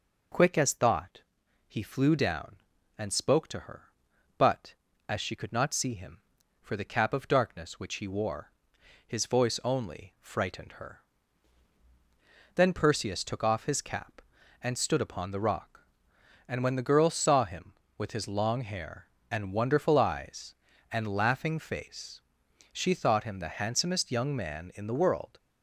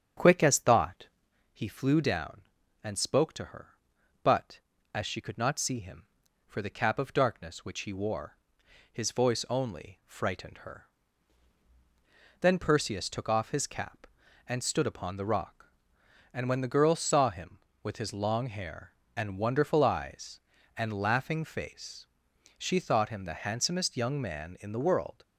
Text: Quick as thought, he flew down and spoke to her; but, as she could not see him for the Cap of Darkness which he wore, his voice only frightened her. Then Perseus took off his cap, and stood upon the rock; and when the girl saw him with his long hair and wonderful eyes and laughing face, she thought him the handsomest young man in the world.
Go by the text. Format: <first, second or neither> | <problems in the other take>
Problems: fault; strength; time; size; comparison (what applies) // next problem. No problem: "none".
first | starts louder than the rest; strong; until 1.5 s; 8 dB